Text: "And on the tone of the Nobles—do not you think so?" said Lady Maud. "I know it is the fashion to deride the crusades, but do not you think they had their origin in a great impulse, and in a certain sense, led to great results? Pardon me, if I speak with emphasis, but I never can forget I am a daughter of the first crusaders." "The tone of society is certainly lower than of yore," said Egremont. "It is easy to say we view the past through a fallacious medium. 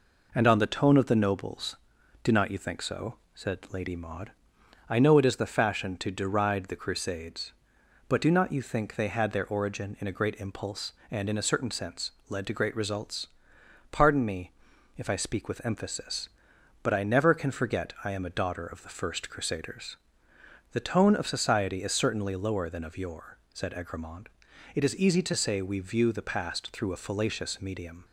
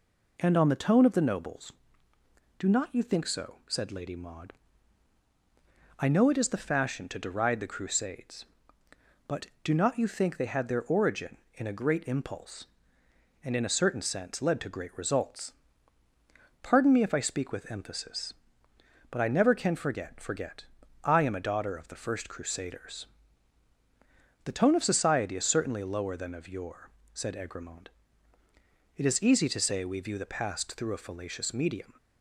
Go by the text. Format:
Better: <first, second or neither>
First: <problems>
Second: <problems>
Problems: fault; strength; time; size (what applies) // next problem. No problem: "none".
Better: first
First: none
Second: says "forget" twice; at 20.2 s